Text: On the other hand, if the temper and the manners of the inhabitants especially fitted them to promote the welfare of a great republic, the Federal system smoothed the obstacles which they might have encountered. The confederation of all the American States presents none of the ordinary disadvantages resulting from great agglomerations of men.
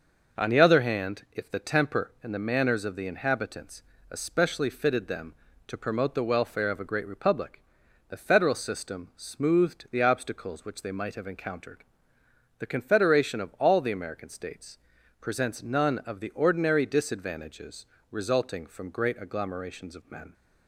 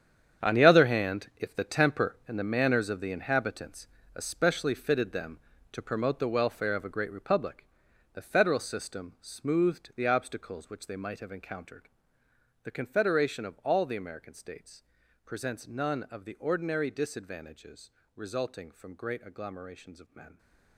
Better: first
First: pauses between "inhabitants" and "especially"; slight; at 3.8 s; 0.28 s long // pauses between "States" and "presents"; at 14.7 s; 0.44 s long // pauses between "disadvantages" and "resulting"; slight; at 17.8 s; 0.26 s long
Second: gets quieter; strong; throughout; 12.5 dB // pauses between "inhabitants" and "especially"; slight; at 3.8 s; 0.28 s long // pauses between "States" and "presents"; at 14.8 s; 0.44 s long // pauses between "disadvantages" and "resulting"; slight; at 17.8 s; 0.26 s long

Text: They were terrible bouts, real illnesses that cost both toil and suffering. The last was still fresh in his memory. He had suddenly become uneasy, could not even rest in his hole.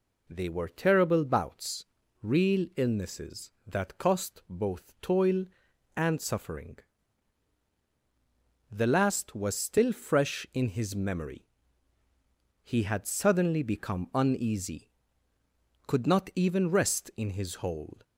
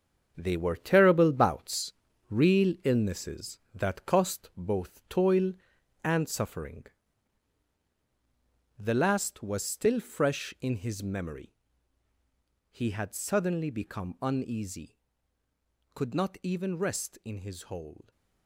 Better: first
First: none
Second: gets quieter; strong; throughout; 9 dB

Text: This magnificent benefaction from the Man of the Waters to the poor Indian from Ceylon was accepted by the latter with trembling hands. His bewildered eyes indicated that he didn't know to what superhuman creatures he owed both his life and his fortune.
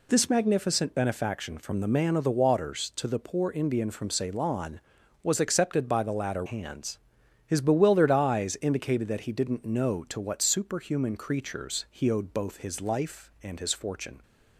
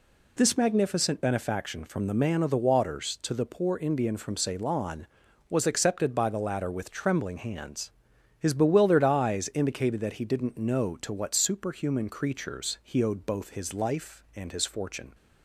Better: second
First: skips "with trembling"; at 6.4 s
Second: none

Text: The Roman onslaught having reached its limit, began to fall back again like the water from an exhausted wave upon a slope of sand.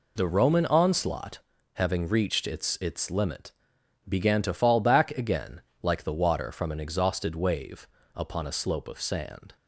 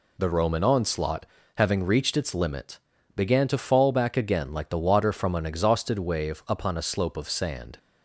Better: second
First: pauses between "onslaught" and "having"; slight; at 1.3 s; 0.36 s long // says "its" twice; at 2.8 s // pauses between "again" and "like"; slight; at 5.5 s; 0.22 s long // pauses between "wave" and "upon"; slight; at 7.8 s; 0.30 s long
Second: pauses between "onslaught" and "having"; slight; at 1.2 s; 0.32 s long

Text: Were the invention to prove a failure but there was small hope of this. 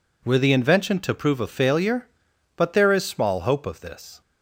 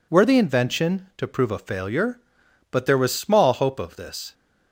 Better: second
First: says "is" for "was"; at 2.9 s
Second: none

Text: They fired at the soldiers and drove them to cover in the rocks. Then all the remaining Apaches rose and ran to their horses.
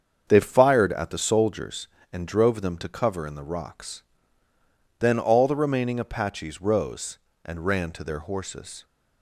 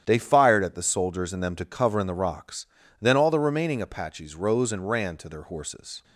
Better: first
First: starts louder than the rest; strong; until 1.2 s; 7 dB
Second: starts louder than the rest; strong; until 1.0 s; 9.5 dB // skips "drove"; at 1.4 s

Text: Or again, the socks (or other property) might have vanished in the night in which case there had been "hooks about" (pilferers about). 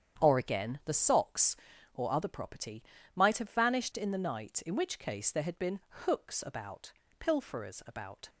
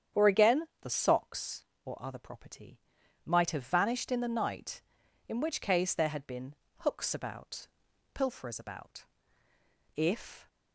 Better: first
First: starts louder than the rest; strong; until 1.2 s; 8.5 dB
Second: starts louder than the rest; strong; until 1.2 s; 8.5 dB // pauses between "been" and "hooks"; slight; at 6.5 s; 0.24 s long // goes on to say "If"; from 9.9 s on; 0.52 s long

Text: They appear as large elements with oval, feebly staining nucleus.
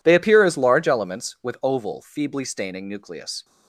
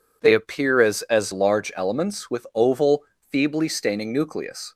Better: first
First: none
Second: says "as" twice; at 1.0 s

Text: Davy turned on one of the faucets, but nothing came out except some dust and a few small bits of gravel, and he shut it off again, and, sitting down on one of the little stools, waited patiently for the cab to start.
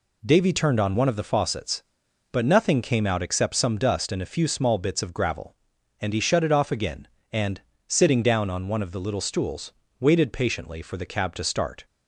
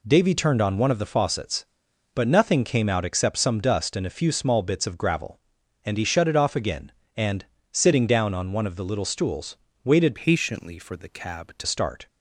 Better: first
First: none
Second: changes voice from "patiently" to "to"; from 10.1 to 11.6 s; 1.5 s long

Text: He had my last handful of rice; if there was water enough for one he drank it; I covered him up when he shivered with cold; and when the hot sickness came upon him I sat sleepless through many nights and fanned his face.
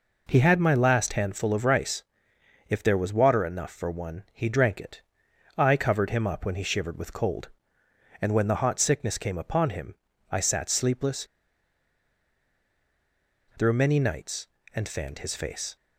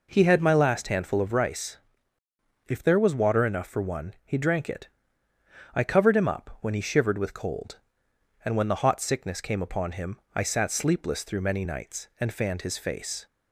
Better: second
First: pauses between "him" and "I"; slight; at 9.9 s; 0.34 s long // pauses between "sleepless" and "through"; strong; at 11.2 s; 2.3 s long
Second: pauses between "him" and "I"; slight; at 10.1 s; 0.16 s long

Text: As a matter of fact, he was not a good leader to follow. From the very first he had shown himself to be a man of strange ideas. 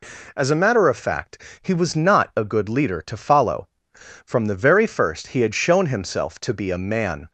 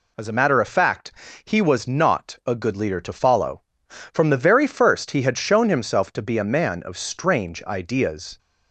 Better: second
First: stops before "of strange ideas"; at 7.2 s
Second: none

